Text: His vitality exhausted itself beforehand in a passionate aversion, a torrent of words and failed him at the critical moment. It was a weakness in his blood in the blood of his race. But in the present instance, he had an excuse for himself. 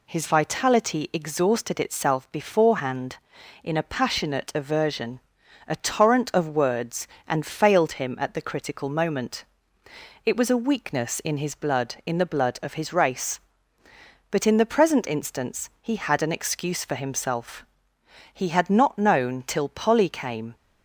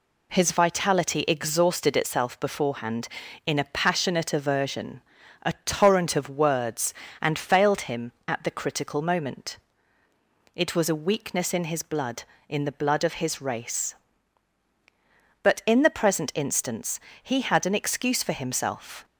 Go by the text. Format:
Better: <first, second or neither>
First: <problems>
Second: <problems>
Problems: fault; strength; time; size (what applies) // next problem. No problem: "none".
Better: second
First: goes on to say "He had not known till Polly came"; strong; from 18.3 s on; 2.2 s long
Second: none